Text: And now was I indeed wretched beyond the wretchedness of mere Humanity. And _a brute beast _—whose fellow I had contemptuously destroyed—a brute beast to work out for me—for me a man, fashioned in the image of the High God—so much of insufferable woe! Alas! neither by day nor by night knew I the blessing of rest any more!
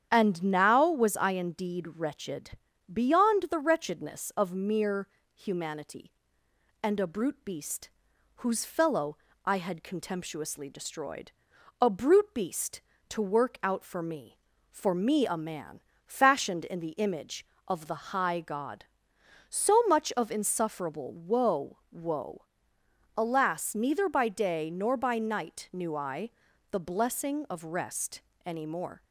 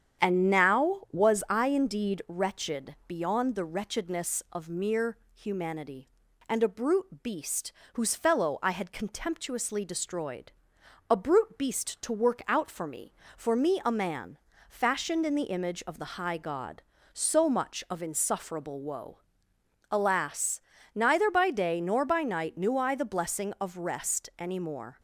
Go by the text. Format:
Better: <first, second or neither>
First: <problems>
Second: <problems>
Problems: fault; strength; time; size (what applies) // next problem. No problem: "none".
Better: second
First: starts louder than the rest; strong; until 1.1 s; 9 dB // pauses between "wretched" and "beyond"; at 2.5 s; 0.40 s long // pauses between "mere" and "Humanity"; slight; at 5.0 s; 0.32 s long // pauses between "fellow" and "I"; slight; at 9.1 s; 0.28 s long // says "woe" twice; at 21.9 s // pauses between "I" and "the"; at 26.3 s; 0.40 s long // pauses between "rest" and "any"; slight; at 28.2 s; 0.22 s long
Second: starts louder than the rest; strong; until 1.3 s; 8.5 dB // pauses between "mere" and "Humanity"; slight; at 5.1 s; 0.16 s long